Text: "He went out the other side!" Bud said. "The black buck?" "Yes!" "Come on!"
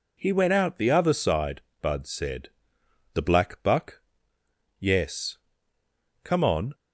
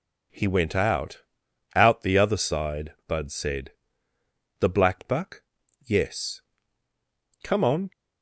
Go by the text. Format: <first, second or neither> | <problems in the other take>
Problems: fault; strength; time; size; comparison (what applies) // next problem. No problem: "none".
first | says "out" twice; at 1.7 s